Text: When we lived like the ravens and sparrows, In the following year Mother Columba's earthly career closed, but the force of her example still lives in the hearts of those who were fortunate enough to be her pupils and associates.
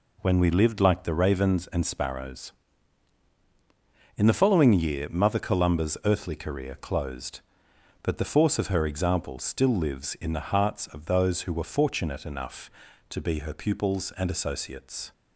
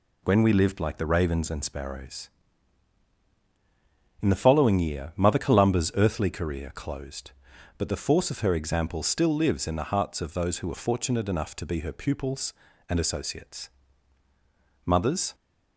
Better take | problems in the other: first | goes on to say "Mothers"; from 14.8 s on; 0.50 s long

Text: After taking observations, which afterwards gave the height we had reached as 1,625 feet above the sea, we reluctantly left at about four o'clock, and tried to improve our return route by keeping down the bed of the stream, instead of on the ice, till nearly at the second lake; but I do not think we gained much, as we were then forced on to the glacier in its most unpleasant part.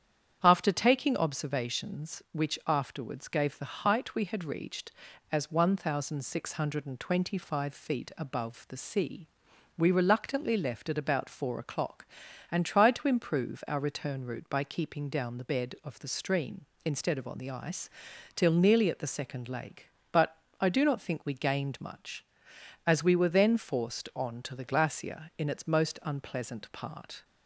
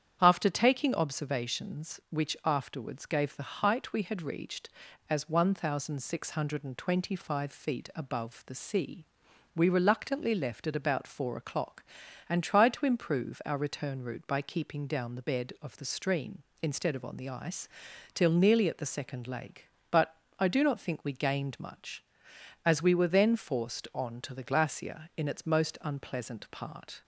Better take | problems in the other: neither | starts louder than the rest; strong; the same in both // pauses between "but" and "I"; slight; the same in both

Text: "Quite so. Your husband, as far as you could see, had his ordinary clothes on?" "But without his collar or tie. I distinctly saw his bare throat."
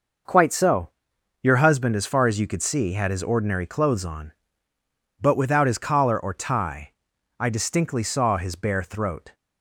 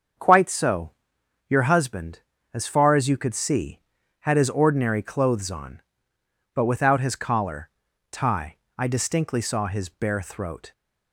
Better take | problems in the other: first | starts louder than the rest; until 1.7 s; 7 dB // skips "or"; at 7.8 s

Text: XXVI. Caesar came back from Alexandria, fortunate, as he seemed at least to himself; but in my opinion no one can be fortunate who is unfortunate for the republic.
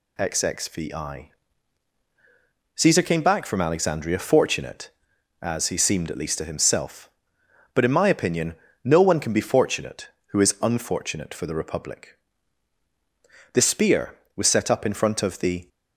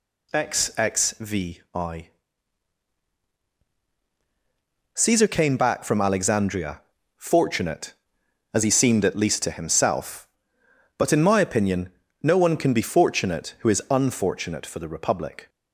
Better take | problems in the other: second | pauses between "opinion" and "no"; slight; at 8.5 s; 0.28 s long; slight in the second // goes on to say "The spear was set up in front of the"; strong; from 13.5 s on; 2.1 s long

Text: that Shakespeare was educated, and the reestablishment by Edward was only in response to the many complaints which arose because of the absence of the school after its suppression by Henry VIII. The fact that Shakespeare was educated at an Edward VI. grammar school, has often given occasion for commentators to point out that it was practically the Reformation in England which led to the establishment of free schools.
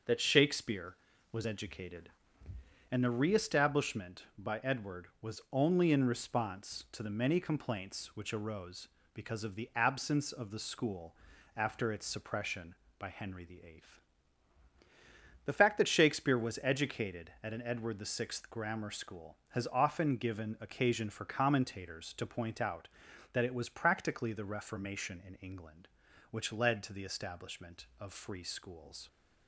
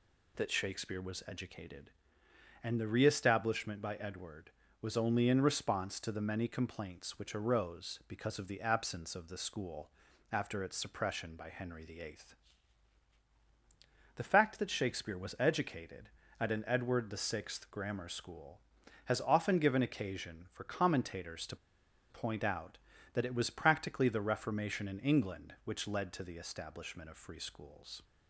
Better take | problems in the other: first | pauses between "school" and "after"; at 9.8 s; 0.42 s long; also in the first // pauses between "to" and "point"; noticeable; at 21.5 s; 0.54 s long

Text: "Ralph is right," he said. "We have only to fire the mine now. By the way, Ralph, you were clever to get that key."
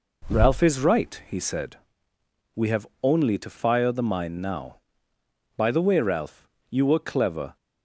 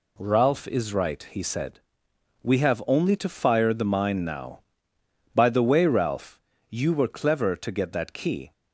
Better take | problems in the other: second | pauses between "have" and "only"; slight; at 2.8 s; 0.16 s long // stops before "to get that key"; at 7.5 s

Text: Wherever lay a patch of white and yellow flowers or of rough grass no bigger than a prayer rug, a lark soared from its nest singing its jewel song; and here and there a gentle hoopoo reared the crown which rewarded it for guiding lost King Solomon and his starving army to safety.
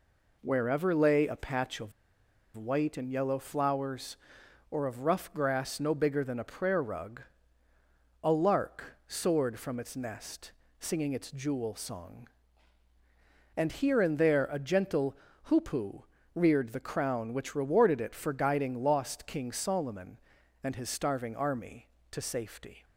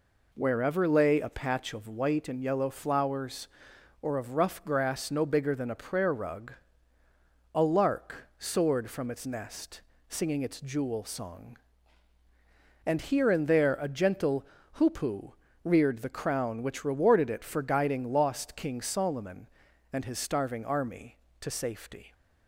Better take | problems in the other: second | pauses between "of" and "white"; noticeable; at 1.9 s; 0.64 s long // pauses between "nest" and "singing"; slight; at 10.5 s; 0.32 s long; slight in the second // pauses between "gentle" and "hoopoo"; slight; at 15.1 s; 0.28 s long; slight in the second // pauses between "hoopoo" and "reared"; slight; at 16.0 s; 0.32 s long; slight in the second

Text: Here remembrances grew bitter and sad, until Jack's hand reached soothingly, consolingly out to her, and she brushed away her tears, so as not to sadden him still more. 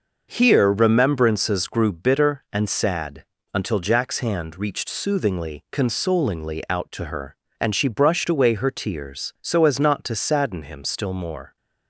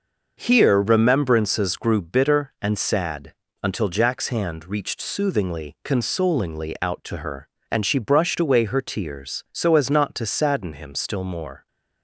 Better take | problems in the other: neither | starts louder than the rest; noticeable; the same in both

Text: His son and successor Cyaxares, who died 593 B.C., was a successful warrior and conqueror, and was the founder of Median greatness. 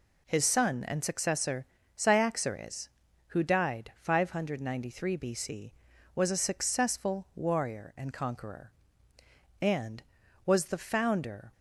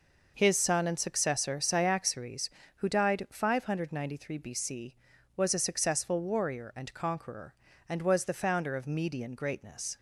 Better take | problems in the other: second | pauses between "successor" and "Cyaxares"; slight; at 1.6 s; 0.30 s long // stops before "of Median greatness"; at 11.5 s

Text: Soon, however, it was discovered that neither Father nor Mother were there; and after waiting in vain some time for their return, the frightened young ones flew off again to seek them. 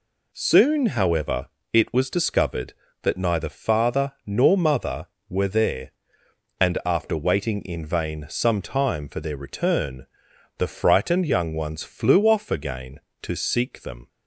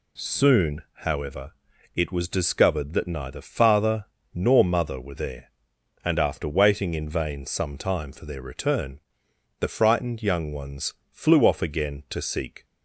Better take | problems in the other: first | pauses between "Father" and "nor"; slight; at 4.0 s; 0.26 s long // pauses between "ones" and "flew"; slight; at 10.9 s; 0.16 s long // stops before "them"; at 12.6 s

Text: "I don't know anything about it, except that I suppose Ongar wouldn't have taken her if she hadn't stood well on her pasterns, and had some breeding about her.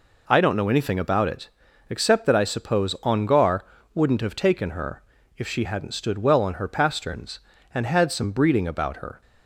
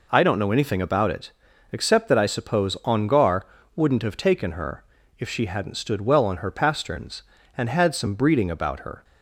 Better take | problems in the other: neither | pauses between "Ongar" and "wouldn't"; slight; the same in both // pauses between "her" and "if"; slight; the same in both

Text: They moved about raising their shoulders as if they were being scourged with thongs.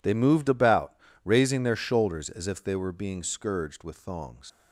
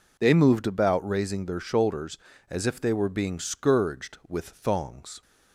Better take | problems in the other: second | pauses between "about" and "raising"; slight; at 0.9 s; 0.28 s long // leaves "thongs" unfinished; at 4.4 s; 100 ms

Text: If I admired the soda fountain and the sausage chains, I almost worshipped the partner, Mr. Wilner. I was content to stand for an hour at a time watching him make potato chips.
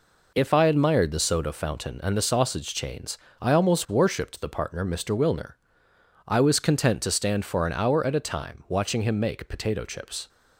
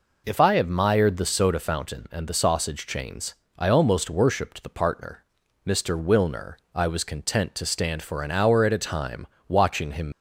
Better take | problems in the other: first | pauses between "time" and "watching"; slight; at 9.2 s; 0.22 s long // stops before "make potato chips"; at 10.1 s

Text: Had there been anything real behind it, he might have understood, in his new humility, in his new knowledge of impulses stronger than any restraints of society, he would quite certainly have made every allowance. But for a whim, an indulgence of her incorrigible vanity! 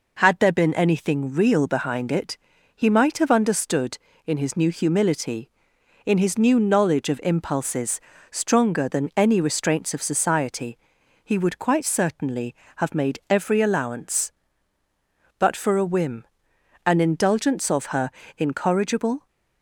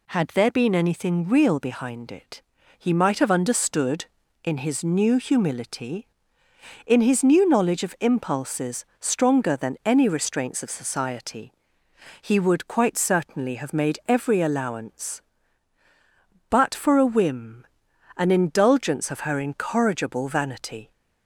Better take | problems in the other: second | pauses between "impulses" and "stronger"; slight; at 7.9 s; 0.32 s long // pauses between "her" and "incorrigible"; slight; at 18.0 s; 0.30 s long // stops before "vanity"; at 19.2 s

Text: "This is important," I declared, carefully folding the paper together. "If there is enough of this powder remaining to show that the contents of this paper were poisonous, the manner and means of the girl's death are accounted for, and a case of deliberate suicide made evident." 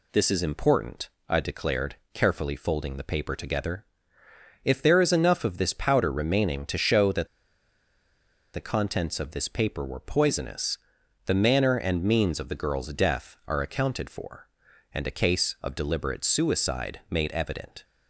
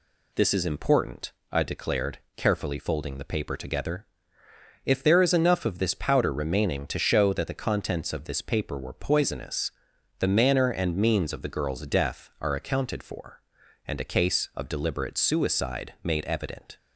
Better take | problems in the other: second | pauses between "that" and "the"; strong; at 7.2 s; 1.2 s long

